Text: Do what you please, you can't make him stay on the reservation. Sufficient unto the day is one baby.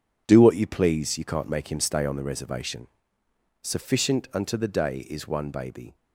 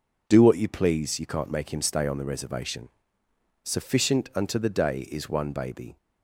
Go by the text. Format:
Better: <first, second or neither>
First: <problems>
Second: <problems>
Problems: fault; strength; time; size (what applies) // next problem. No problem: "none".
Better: second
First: gets quieter; strong; throughout; 9 dB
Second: none